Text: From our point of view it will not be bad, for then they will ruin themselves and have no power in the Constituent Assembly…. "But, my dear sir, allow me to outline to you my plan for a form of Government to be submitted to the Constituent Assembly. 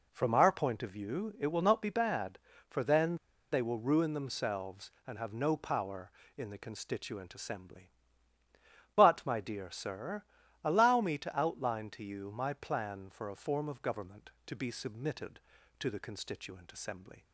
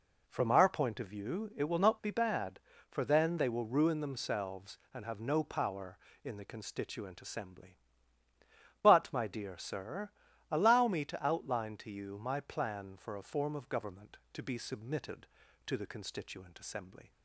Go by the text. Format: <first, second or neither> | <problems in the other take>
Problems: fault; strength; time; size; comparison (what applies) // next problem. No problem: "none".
second | pauses between "then" and "they"; at 3.1 s; 0.36 s long